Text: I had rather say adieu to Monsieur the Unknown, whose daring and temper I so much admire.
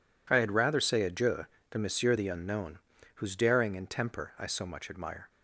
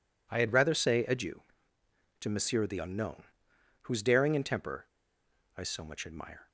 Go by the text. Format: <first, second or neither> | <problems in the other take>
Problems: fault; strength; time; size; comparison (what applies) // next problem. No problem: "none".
first | pauses between "temper" and "I"; noticeable; at 4.8 s; 0.71 s long